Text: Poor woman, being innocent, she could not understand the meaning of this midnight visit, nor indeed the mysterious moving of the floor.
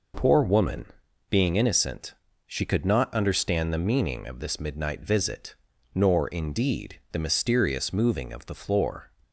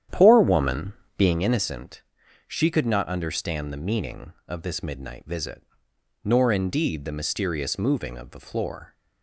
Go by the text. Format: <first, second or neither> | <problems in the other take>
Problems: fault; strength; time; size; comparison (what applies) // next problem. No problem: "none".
first | starts louder than the rest; strong; until 1.5 s; 10 dB